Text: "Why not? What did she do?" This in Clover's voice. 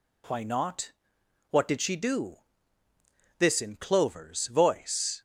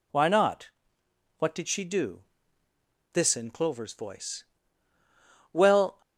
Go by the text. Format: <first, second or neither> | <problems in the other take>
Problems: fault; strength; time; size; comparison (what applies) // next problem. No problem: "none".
first | goes on to say "Well"; slight; from 5.5 s on; 0.48 s long